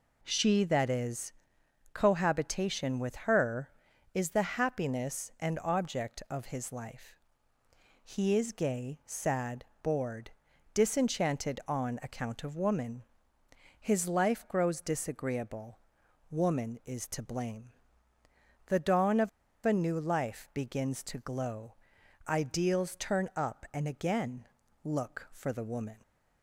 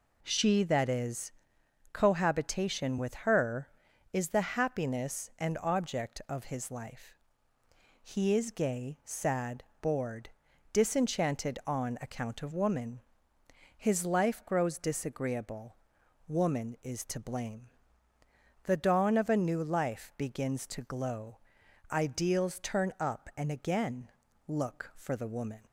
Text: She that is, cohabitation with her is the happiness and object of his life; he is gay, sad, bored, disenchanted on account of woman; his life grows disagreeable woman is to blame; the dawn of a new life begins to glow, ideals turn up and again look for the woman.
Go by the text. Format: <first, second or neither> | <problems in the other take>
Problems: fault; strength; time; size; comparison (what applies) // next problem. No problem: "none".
second | pauses between "disagreeable" and "woman"; noticeable; at 15.7 s; 0.52 s long; noticeable in the second // pauses between "of" and "a"; at 19.2 s; 0.36 s long // pauses between "again" and "look"; at 24.4 s; 0.38 s long; also in the second